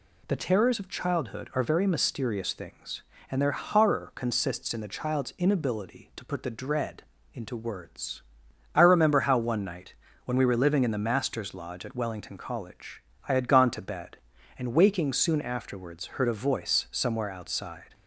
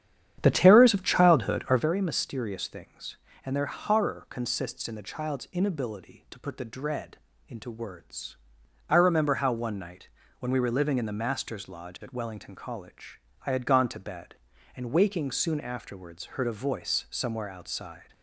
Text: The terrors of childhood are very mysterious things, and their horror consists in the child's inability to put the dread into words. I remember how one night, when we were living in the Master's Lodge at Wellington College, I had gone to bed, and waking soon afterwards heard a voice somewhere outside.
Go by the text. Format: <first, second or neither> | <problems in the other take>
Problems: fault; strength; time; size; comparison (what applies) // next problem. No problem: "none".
first | starts louder than the rest; strong; until 1.9 s; 9.5 dB // pauses between "dread" and "into"; slight; at 7.1 s; 0.32 s long; slight in the first